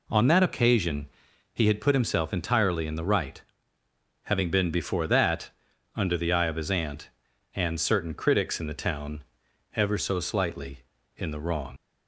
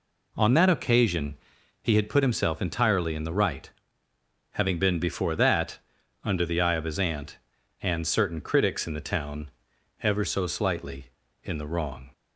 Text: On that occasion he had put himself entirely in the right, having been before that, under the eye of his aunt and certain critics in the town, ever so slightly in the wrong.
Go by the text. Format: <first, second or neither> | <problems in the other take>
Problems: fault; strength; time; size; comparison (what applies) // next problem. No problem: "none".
second | pauses between "occasion" and "he"; at 1.0 s; 0.44 s long; also in the second // leaves "wrong" unfinished; at 11.7 s; 90 ms